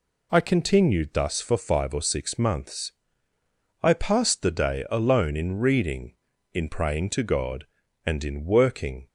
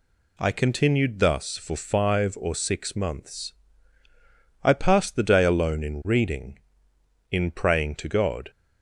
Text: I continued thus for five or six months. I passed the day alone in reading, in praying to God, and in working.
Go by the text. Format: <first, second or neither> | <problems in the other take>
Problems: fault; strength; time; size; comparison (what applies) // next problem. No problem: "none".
first | stops before "and in working"; at 8.5 s